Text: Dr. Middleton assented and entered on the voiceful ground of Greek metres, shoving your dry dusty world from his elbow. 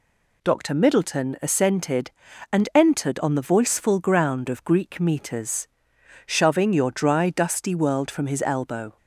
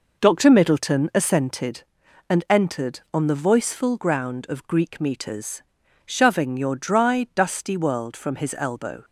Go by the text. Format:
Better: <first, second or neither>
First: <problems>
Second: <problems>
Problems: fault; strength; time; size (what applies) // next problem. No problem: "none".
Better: first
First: none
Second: starts louder than the rest; noticeable; until 1.9 s; 5 dB